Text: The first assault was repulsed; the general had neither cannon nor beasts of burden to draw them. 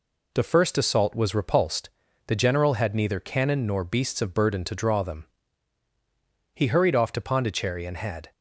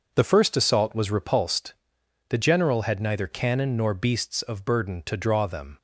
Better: second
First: goes on to say "He hurried off to Pondicherry and had"; strong; from 6.5 s on; 1.7 s long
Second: none

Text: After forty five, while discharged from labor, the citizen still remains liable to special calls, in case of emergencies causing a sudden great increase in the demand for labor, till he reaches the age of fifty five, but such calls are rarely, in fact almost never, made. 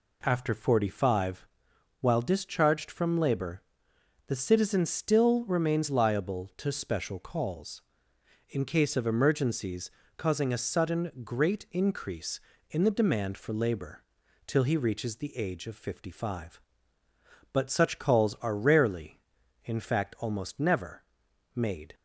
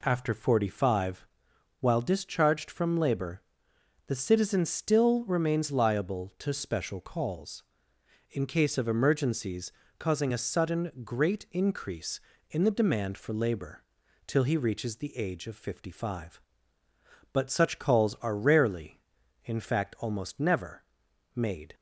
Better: neither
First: pauses between "emergencies" and "causing"; slight; at 9.9 s; 0.28 s long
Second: pauses between "emergencies" and "causing"; slight; at 9.7 s; 0.28 s long

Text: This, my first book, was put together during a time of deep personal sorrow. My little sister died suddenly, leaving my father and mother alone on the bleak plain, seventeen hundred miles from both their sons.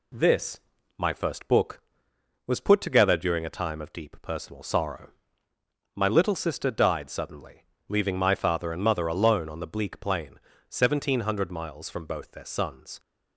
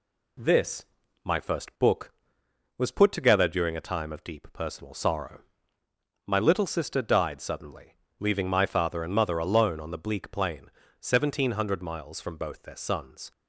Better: neither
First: none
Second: none

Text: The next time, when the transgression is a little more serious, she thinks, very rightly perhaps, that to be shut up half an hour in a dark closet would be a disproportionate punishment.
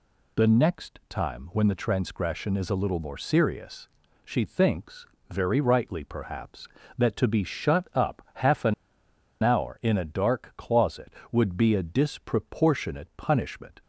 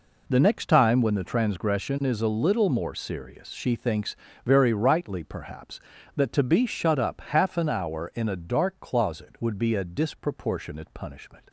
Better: second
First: pauses between "an" and "hour"; noticeable; at 8.7 s; 0.69 s long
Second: none

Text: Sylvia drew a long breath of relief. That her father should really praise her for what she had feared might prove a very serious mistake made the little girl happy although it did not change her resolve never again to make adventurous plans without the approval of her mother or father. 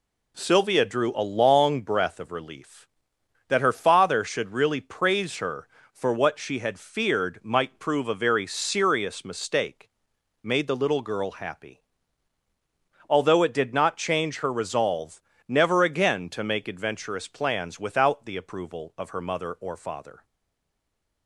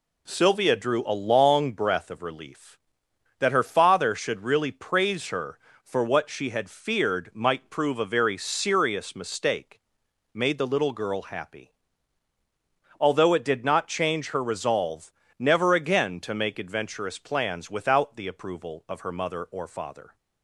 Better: second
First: pauses between "mistake" and "made"; noticeable; at 9.8 s; 0.54 s long // pauses between "happy" and "although"; strong; at 11.7 s; 1.2 s long // pauses between "resolve" and "never"; slight; at 15.2 s; 0.26 s long // stays silent after the last word; from 20.2 s on; 1.0 s long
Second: pauses between "mistake" and "made"; noticeable; at 9.8 s; 0.54 s long // pauses between "happy" and "although"; strong; at 11.7 s; 1.2 s long // pauses between "resolve" and "never"; slight; at 15.1 s; 0.26 s long

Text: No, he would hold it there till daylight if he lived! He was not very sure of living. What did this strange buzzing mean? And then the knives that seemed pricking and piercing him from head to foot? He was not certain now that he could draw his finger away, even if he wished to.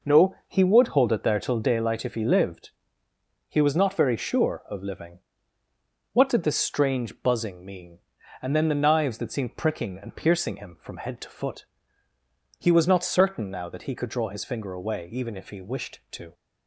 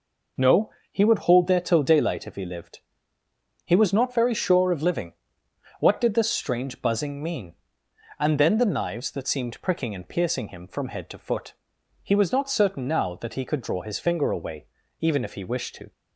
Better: first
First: none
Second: skips "it"; at 1.4 s

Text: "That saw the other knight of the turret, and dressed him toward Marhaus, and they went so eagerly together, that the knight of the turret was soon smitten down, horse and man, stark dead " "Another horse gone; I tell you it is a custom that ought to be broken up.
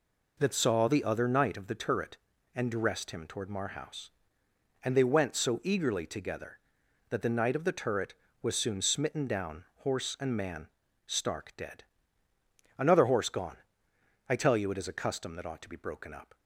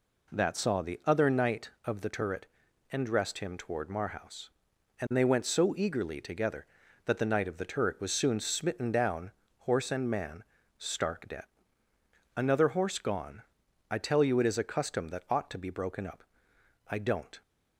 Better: first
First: none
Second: goes on to say "I don't"; from 16.8 s on; 0.54 s long

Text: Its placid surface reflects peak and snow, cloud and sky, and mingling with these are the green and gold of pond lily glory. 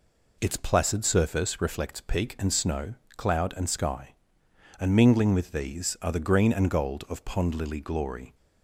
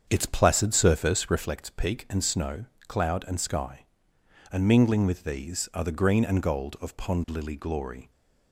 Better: first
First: none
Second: starts louder than the rest; strong; until 1.5 s; 7 dB

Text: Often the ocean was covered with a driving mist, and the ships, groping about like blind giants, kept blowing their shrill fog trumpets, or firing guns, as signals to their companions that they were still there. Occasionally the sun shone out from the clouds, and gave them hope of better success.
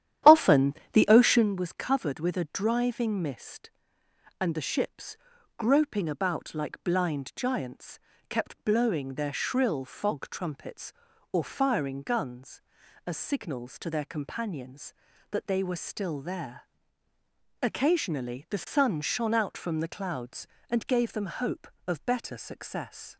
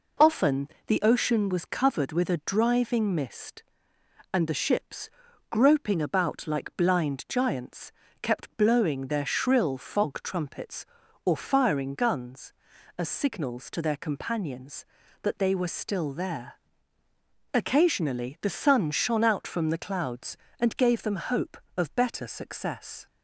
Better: second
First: starts louder than the rest; strong; until 1.5 s; 11 dB // pauses between "Often" and "the"; slight; at 0.7 s; 0.20 s long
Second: pauses between "Often" and "the"; slight; at 0.6 s; 0.20 s long

